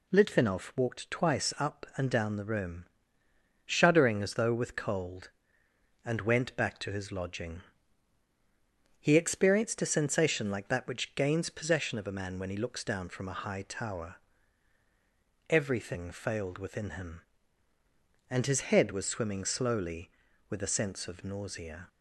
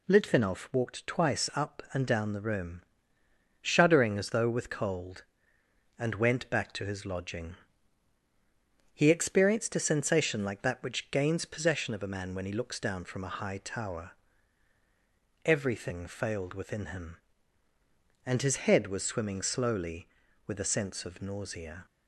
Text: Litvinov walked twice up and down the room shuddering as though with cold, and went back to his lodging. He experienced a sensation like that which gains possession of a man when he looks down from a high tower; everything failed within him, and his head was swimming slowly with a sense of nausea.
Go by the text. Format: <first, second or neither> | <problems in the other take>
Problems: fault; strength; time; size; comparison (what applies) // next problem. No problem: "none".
neither | pauses between "room" and "shuddering"; noticeable; the same in both